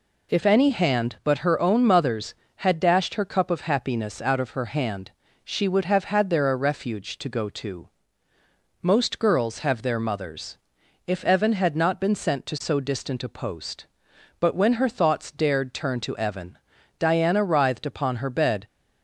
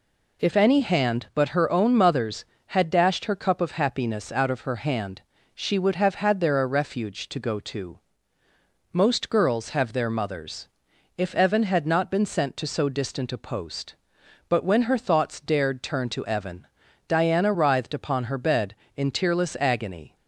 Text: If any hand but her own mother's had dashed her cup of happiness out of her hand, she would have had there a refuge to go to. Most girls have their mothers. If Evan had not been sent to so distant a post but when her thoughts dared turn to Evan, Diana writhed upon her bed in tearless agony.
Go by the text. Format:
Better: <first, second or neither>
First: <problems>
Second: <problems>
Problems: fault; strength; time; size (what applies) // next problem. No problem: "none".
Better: second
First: stops before "in tearless agony"; at 18.6 s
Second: none